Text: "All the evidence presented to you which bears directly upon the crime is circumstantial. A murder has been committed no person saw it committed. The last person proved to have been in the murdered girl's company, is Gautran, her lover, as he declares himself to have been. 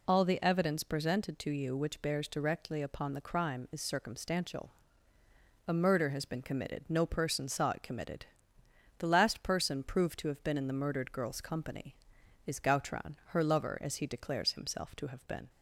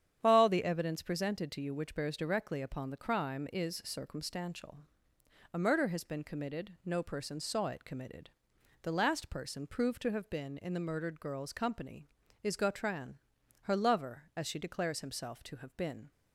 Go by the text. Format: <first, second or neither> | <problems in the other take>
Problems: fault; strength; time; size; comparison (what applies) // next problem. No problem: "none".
first | starts louder than the rest; strong; until 1.2 s; 9 dB // says "she" for "he"; at 14.4 s